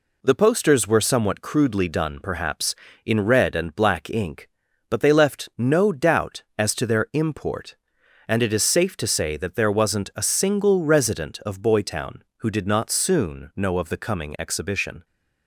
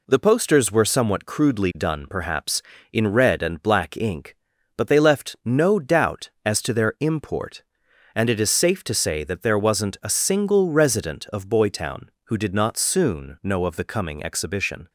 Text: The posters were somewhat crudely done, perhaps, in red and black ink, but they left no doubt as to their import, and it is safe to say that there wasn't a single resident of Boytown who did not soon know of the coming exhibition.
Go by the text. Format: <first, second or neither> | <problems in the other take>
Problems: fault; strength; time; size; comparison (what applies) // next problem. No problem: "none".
neither | none